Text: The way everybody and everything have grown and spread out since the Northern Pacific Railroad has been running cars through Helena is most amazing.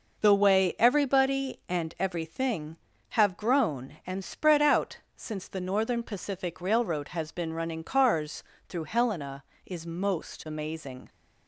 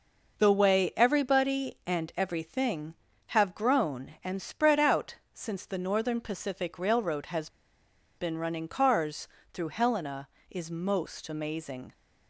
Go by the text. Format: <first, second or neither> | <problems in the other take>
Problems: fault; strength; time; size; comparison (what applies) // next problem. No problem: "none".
first | pauses between "out" and "since"; slight; at 5.1 s; 0.18 s long; slight in the first // pauses between "has" and "been"; noticeable; at 7.4 s; 0.69 s long // pauses between "cars" and "through"; slight; at 9.2 s; 0.26 s long; slight in the first